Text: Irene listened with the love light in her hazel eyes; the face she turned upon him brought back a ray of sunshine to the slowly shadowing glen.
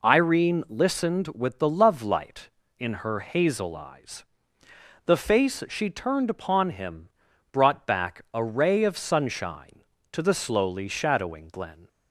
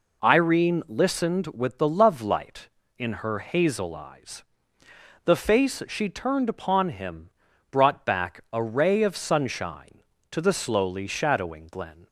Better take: neither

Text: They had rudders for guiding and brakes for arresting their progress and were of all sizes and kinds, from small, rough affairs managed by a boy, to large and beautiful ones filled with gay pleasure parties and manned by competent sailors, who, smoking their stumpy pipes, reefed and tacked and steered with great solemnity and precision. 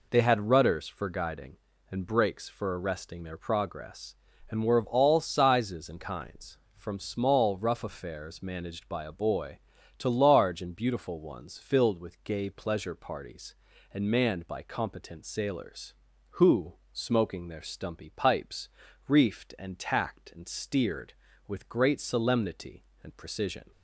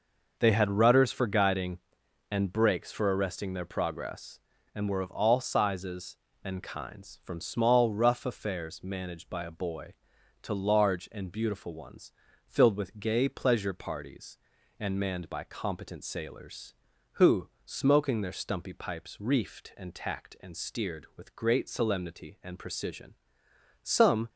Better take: first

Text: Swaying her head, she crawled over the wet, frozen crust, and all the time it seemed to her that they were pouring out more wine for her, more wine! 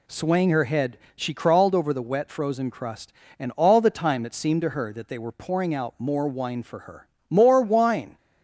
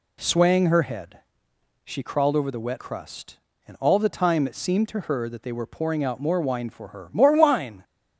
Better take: first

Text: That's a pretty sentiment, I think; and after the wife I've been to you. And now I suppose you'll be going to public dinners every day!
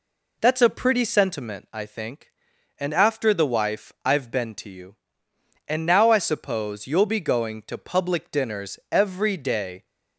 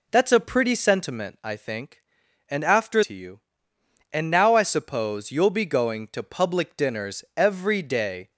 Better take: first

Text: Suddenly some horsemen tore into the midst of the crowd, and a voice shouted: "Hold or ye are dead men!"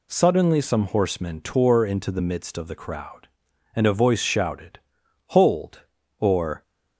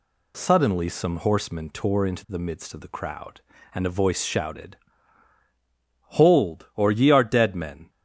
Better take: second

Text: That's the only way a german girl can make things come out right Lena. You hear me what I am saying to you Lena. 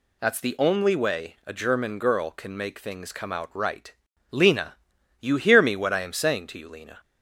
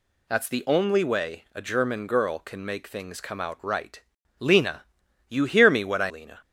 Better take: first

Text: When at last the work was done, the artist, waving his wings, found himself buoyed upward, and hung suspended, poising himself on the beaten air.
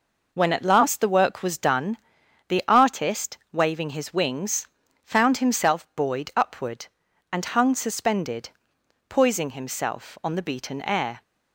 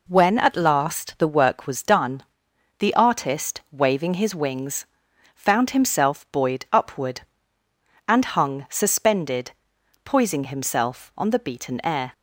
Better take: neither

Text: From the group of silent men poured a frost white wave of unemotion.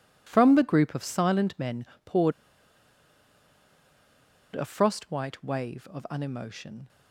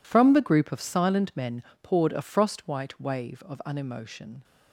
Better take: second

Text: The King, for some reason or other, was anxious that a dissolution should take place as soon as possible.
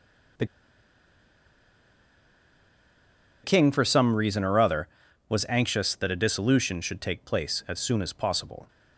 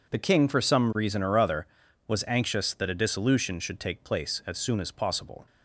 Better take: second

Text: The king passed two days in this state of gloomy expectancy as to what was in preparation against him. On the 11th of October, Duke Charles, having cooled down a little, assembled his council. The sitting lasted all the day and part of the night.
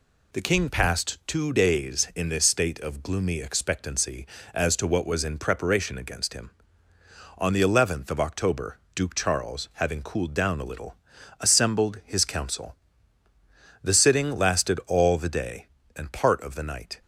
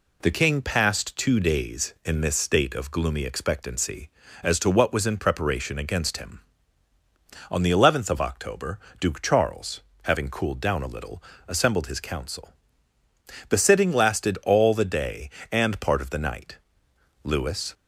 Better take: first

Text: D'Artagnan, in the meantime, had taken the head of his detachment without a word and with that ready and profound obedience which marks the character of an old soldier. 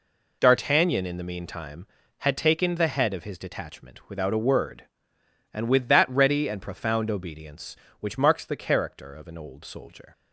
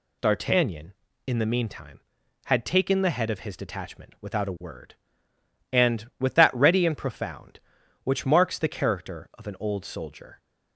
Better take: first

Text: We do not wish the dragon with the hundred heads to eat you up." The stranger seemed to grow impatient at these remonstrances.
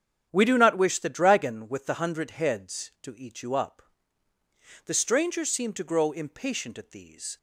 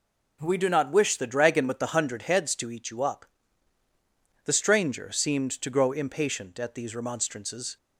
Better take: second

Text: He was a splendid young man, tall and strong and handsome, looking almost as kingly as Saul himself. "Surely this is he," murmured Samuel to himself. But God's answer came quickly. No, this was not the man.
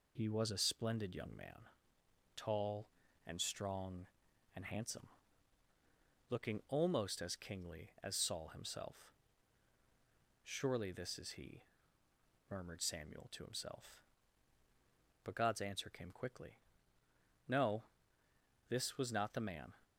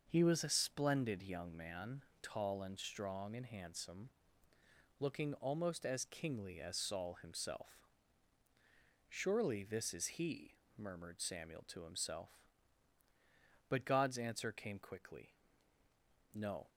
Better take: first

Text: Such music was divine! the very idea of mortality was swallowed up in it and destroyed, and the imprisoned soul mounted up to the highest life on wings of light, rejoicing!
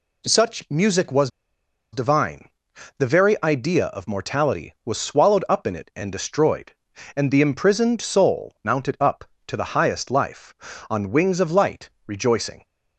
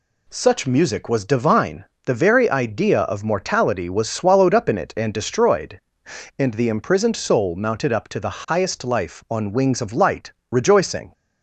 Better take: second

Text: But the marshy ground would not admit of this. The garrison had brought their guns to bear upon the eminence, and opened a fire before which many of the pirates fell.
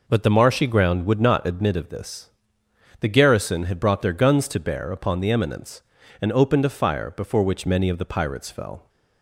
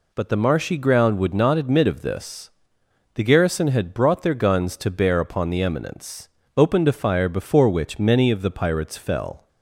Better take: first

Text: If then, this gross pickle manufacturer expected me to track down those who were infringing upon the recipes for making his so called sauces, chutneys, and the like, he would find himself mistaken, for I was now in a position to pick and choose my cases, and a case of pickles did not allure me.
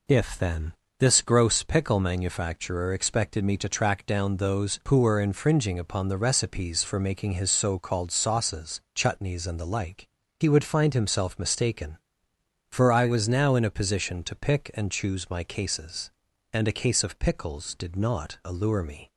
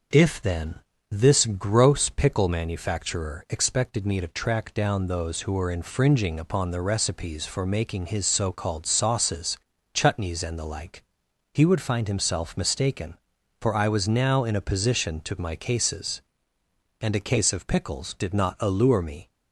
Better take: first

